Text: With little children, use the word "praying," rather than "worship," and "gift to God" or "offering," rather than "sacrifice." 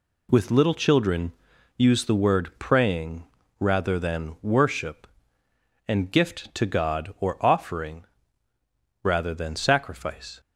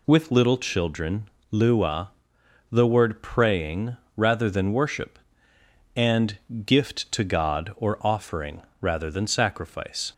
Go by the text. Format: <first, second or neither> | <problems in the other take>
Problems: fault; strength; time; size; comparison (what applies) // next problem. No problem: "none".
first | says "lua" for "use"; at 1.5 s // pauses between "and" and "gift"; slight; at 6.3 s; 0.30 s long